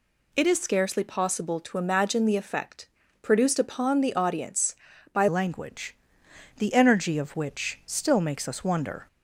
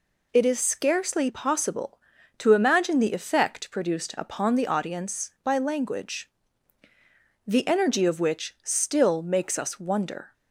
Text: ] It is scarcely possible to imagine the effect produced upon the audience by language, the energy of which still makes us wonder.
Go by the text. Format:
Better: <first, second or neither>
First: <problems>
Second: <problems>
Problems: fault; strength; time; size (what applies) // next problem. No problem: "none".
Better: second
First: pauses between "effect" and "produced"; slight; at 2.8 s; 0.34 s long // changes voice at "language"; from 5.2 s on; 3.8 s long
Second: none